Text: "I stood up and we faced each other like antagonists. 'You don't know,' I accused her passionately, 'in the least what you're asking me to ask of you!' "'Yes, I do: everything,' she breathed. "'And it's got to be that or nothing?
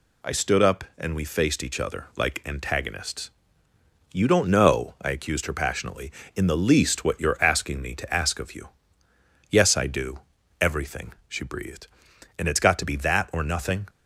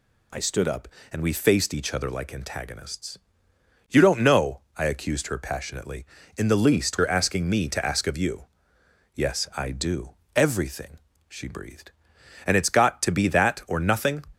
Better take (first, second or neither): first